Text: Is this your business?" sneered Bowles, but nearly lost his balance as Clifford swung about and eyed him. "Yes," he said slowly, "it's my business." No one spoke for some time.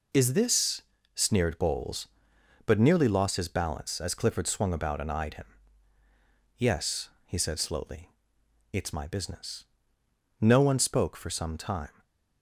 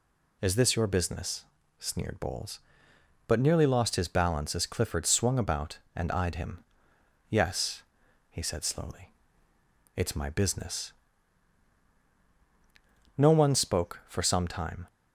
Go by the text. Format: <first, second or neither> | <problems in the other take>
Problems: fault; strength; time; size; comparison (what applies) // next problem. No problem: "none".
second | skips "your business"; at 0.9 s // stays silent after the last word; slight; from 11.9 s on; 0.5 s long